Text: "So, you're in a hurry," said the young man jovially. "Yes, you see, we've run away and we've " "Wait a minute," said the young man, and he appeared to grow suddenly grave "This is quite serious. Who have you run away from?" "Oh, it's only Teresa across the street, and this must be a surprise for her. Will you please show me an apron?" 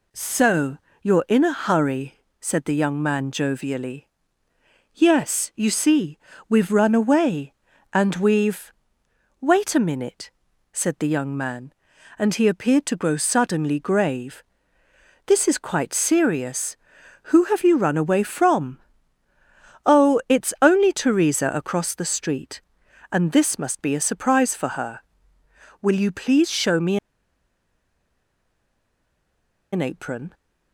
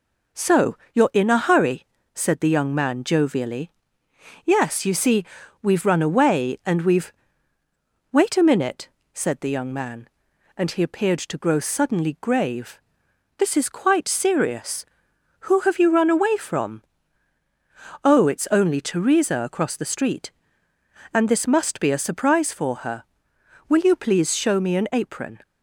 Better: second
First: pauses between "grave" and "This"; noticeable; at 14.4 s; 0.84 s long // pauses between "me" and "an"; strong; at 26.9 s; 2.7 s long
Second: pauses between "grave" and "This"; noticeable; at 12.8 s; 0.56 s long

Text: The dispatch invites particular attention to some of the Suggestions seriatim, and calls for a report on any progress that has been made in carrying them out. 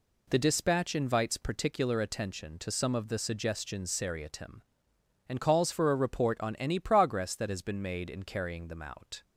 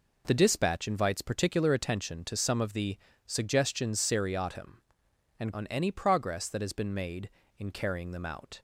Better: first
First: none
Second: pauses between "the" and "Suggestions"; slight; at 2.9 s; 0.30 s long // skips "calls for a report"; at 5.5 s

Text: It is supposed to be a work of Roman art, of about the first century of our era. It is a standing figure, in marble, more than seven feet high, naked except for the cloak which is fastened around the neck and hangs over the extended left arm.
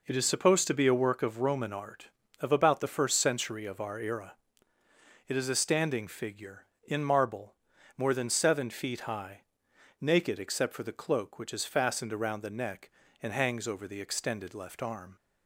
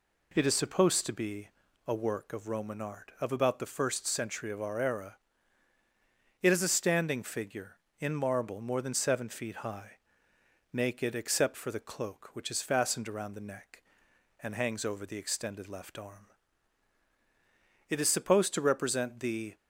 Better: first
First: none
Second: pauses between "be" and "a"; at 1.4 s; 0.38 s long // goes on to say "It is supposed to represent the"; from 17.9 s on; 1.6 s long

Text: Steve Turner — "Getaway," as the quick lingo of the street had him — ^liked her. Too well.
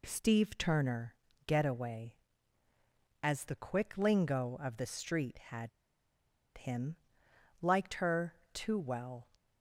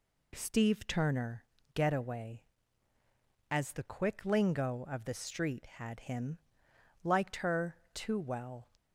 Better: second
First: pauses between "had" and "him"; noticeable; at 5.6 s; 0.88 s long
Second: none

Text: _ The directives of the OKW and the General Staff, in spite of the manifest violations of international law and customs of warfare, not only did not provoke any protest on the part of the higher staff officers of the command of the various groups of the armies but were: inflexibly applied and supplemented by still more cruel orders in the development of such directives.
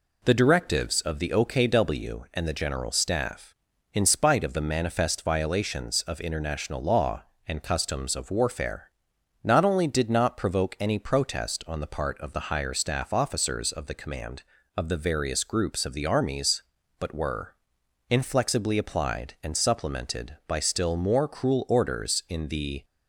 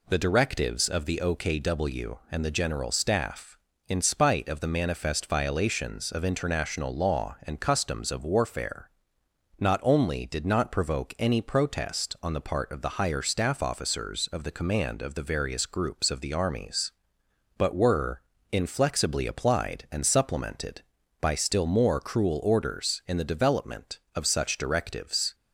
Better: second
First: stops before "development of such directives"; at 22.8 s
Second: none

